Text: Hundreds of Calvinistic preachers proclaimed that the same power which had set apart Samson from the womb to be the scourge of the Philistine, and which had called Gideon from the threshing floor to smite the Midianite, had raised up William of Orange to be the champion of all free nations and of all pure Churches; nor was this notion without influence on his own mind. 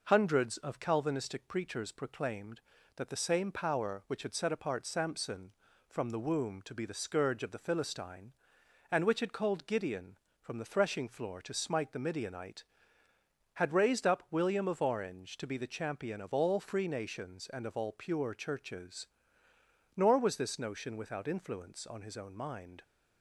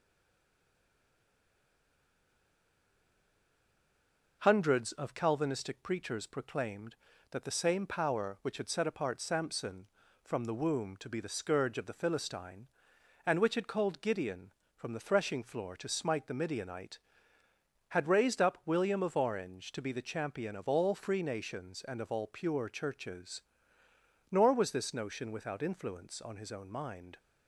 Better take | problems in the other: first | stays silent before the first word; strong; until 4.4 s; 4.4 s long

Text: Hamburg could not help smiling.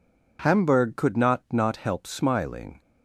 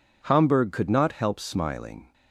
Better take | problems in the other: second | says "not" twice; at 1.5 s

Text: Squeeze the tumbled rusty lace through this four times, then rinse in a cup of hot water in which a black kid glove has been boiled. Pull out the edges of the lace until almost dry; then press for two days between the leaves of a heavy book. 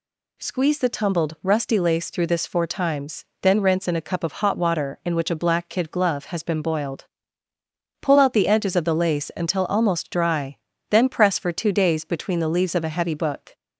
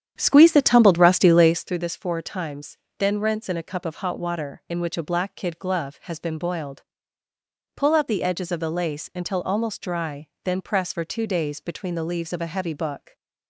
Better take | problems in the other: first | starts louder than the rest; strong; until 1.8 s; 9 dB

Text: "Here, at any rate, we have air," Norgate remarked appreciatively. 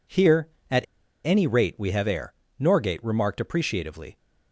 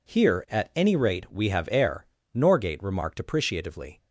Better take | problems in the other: second | pauses between "at" and "any"; at 0.8 s; 0.41 s long

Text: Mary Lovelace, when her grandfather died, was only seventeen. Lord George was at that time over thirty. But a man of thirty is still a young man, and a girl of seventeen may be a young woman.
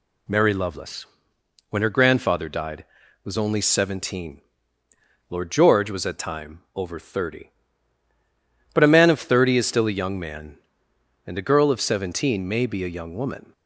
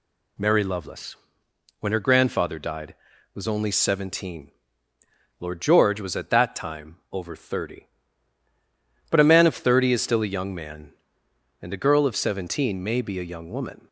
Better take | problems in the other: second | skips "that"; at 6.1 s

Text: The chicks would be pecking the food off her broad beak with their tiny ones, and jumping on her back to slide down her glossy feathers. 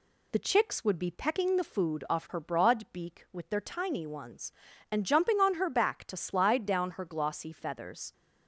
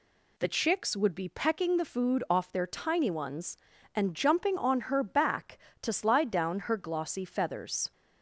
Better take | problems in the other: first | skips "her broad beak with"; at 2.5 s

